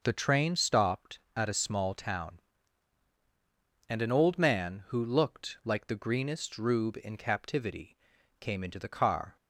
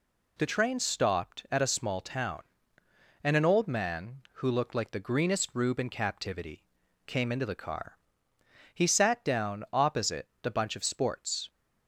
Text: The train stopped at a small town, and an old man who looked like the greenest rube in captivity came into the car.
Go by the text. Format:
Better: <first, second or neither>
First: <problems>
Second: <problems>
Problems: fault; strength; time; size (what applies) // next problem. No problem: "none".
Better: first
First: pauses between "captivity" and "came"; at 7.9 s; 0.44 s long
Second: pauses between "captivity" and "came"; at 6.6 s; 0.44 s long // goes on to say "He sat down opposite the bunch of sports"; strong; from 8.7 s on; 2.7 s long